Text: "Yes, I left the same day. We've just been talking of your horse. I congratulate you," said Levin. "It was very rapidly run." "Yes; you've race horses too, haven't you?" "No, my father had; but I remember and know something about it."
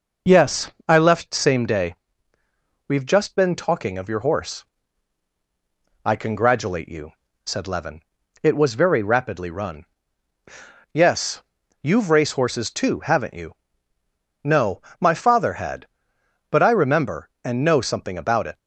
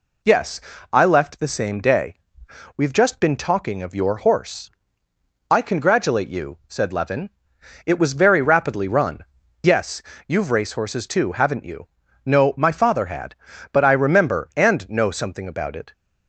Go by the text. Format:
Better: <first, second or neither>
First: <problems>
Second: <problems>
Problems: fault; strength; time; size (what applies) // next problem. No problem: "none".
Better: second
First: skips "the"; at 1.3 s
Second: none